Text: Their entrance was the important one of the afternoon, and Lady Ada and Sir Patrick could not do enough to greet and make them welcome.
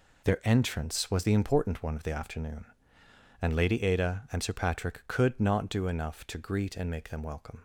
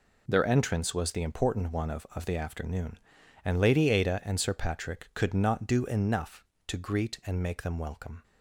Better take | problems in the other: first | says "of" twice; at 2.1 s

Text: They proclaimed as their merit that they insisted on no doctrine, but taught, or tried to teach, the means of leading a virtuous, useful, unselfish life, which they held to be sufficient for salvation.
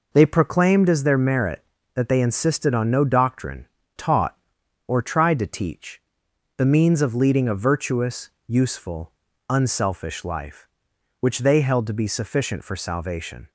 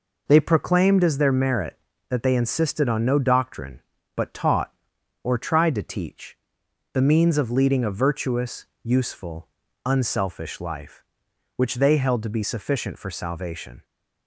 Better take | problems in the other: second | skips "but"; at 3.8 s

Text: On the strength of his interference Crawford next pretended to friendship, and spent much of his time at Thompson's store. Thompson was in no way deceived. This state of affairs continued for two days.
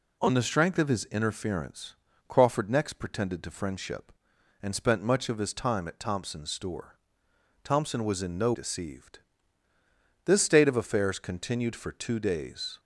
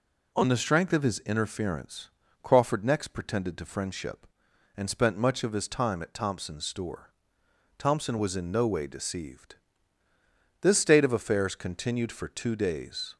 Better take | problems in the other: second | pauses between "interference" and "Crawford"; slight; at 1.9 s; 0.32 s long; slight in the second // skips "way"; at 8.5 s

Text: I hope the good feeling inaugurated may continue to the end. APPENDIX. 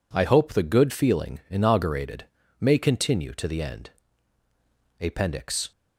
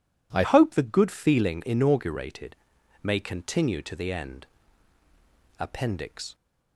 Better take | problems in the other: first | changes voice at "hope"; from 0.4 s on; 5.9 s long // pauses between "inaugurated" and "may"; noticeable; at 2.5 s; 0.48 s long; slight in the first

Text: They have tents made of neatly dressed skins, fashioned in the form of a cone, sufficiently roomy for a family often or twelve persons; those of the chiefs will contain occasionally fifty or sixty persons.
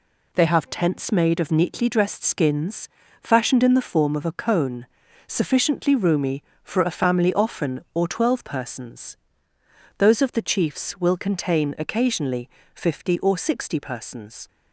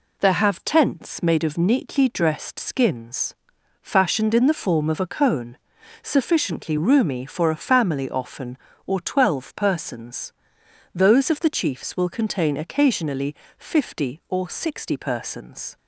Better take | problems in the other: first | says "There" for "They"; at 0.1 s // pauses between "occasionally" and "fifty"; slight; at 13.3 s; 0.24 s long; slight in the first

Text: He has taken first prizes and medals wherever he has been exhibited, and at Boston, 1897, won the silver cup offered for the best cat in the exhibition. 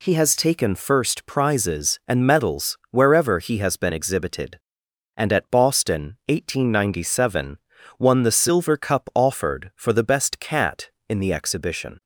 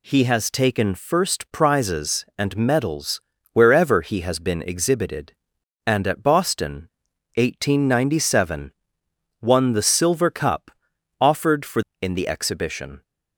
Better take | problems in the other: first | pauses between "medals" and "wherever"; slight; at 3.2 s; 0.30 s long // pauses between "cup" and "offered"; noticeable; at 10.6 s; 0.50 s long // skips "the best cat"; at 11.9 s

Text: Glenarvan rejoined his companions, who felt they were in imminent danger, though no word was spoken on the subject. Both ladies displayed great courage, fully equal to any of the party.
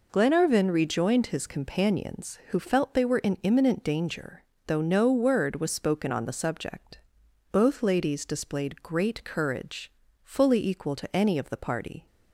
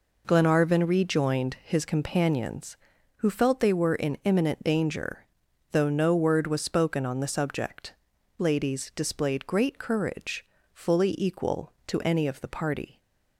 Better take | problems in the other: first | skips "Both"; at 8.1 s

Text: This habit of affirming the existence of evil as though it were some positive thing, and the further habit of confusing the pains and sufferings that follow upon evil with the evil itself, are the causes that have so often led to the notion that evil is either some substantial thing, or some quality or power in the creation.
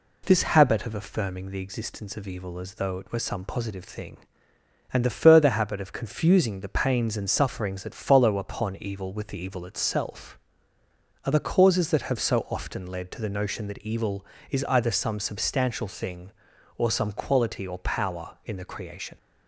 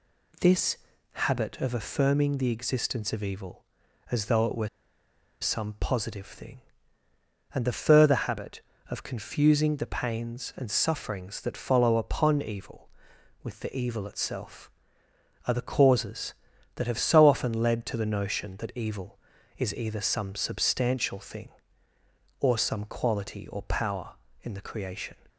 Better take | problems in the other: first | pauses between "This" and "habit"; slight; at 0.7 s; 0.34 s long // pauses between "were" and "some"; noticeable; at 4.6 s; 0.73 s long

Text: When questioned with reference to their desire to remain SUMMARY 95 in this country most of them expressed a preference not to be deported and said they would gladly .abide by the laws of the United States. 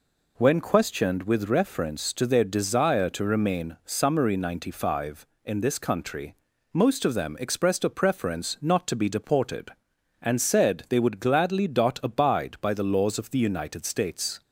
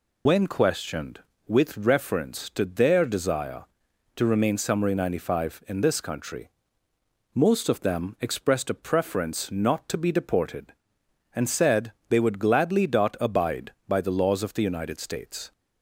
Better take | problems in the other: first | loses the start of "When"; at 0.2 s; 95 ms // pauses between "country" and "most"; noticeable; at 6.4 s; 0.84 s long; also in the first // pauses between "said" and "they"; slight; at 11.9 s; 0.16 s long

